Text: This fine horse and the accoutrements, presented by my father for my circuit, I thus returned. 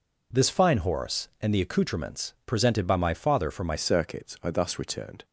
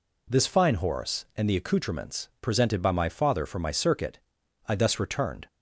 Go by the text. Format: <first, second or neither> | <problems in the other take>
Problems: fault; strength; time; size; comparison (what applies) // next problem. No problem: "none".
second | changes voice at "circuit"; from 3.7 s on; 1.5 s long